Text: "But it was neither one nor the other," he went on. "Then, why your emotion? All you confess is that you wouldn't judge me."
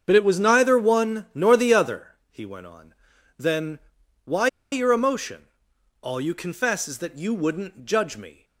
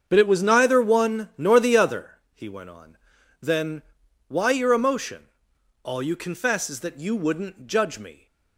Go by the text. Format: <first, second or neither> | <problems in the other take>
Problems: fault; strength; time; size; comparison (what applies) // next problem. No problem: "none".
second | starts louder than the rest; strong; until 1.0 s; 7 dB; strong in the second // pauses between "why" and "your"; slight; at 4.4 s; 0.24 s long